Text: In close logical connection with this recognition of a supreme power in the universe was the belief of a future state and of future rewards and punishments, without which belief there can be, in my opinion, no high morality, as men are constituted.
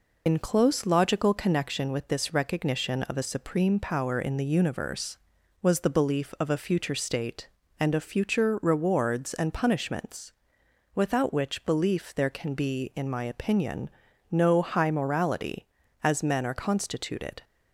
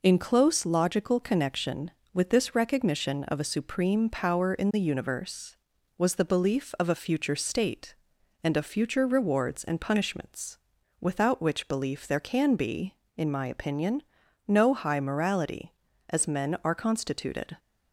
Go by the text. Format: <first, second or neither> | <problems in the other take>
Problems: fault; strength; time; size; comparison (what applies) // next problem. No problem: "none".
second | loses the start of "In"; at 0.2 s; 80 ms